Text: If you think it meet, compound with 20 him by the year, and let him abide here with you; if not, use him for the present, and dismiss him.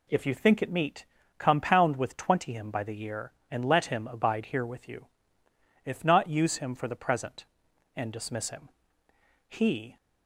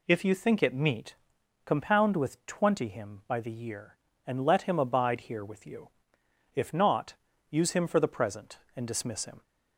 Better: second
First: goes on to say "He"; slight; from 9.4 s on; 0.48 s long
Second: none

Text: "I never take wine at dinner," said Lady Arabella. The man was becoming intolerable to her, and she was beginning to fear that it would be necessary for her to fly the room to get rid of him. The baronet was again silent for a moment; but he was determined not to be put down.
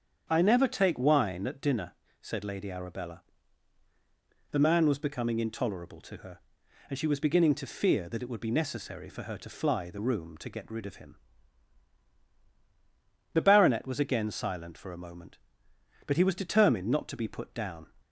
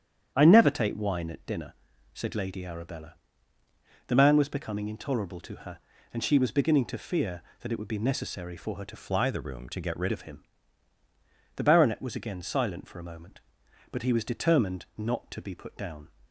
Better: first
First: starts louder than the rest; strong; until 1.3 s; 8 dB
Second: starts louder than the rest; strong; until 1.3 s; 9 dB // changes voice from "fly" to "rid"; from 8.9 to 10.1 s; 1.2 s long

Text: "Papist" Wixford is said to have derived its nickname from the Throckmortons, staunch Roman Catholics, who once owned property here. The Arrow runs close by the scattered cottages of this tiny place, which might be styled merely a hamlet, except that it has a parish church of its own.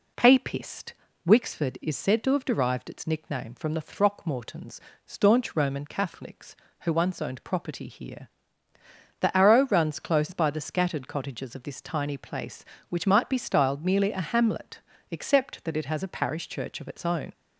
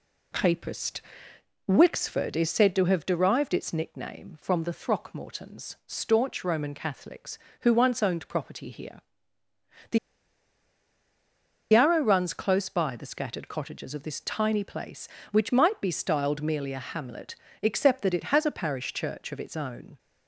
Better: first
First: pauses between "Papist" and "Wixford"; slight; at 0.9 s; 0.34 s long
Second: pauses between "Papist" and "Wixford"; noticeable; at 0.9 s; 0.70 s long // pauses between "The" and "Arrow"; strong; at 9.9 s; 1.7 s long

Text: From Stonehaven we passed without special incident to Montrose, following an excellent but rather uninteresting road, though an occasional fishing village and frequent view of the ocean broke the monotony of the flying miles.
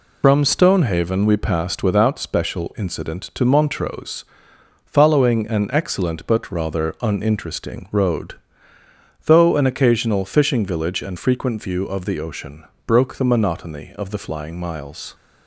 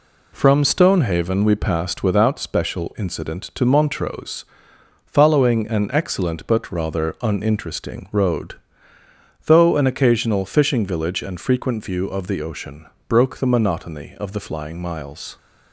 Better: second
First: loses the start of "From"; at 0.2 s; 95 ms // pauses between "ocean" and "broke"; slight; at 12.6 s; 0.22 s long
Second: pauses between "ocean" and "broke"; slight; at 12.8 s; 0.22 s long

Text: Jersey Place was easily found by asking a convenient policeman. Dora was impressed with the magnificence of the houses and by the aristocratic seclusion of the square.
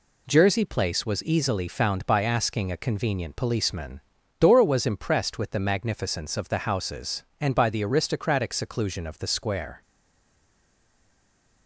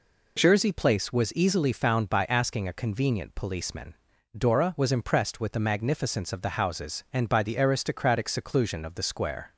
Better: second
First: stays silent after the last word; noticeable; from 9.8 s on; 1.8 s long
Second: none

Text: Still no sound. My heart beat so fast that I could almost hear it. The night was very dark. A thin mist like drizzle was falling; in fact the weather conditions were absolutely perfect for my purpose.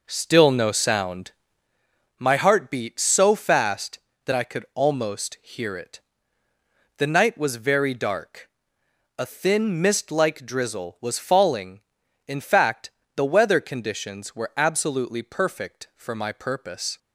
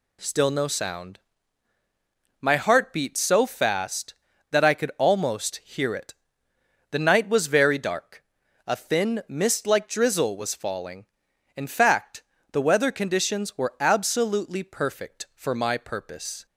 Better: second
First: starts louder than the rest; noticeable; until 1.9 s; 5 dB // pauses between "fact" and "the"; slight; at 12.9 s; 0.26 s long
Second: pauses between "fact" and "the"; slight; at 12.2 s; 0.30 s long

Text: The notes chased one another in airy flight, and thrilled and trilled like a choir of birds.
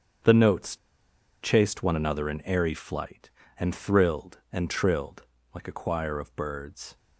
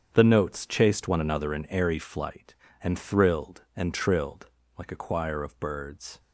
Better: second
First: starts louder than the rest; strong; until 1.8 s; 7.5 dB // pauses between "notes" and "chased"; noticeable; at 0.7 s; 0.65 s long // pauses between "trilled" and "like"; slight; at 5.2 s; 0.28 s long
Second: starts louder than the rest; strong; until 1.1 s; 8 dB // pauses between "trilled" and "like"; slight; at 4.4 s; 0.28 s long

